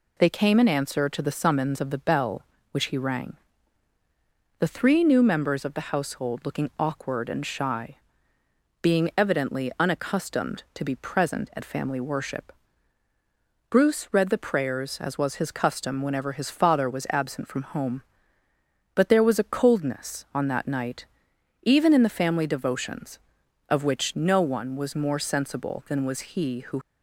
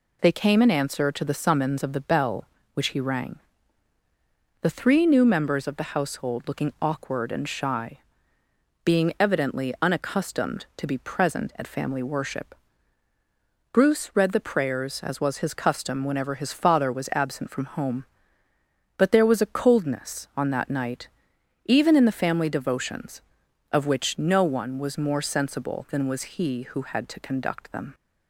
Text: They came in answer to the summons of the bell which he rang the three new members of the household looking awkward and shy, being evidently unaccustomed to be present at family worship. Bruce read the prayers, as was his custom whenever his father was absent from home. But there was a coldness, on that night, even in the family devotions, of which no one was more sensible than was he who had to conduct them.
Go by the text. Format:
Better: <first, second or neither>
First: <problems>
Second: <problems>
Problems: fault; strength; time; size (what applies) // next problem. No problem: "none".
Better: second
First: pauses between "rang" and "the"; at 3.3 s; 1.2 s long // stops before "had to conduct them"; at 26.8 s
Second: pauses between "rang" and "the"; at 3.3 s; 1.2 s long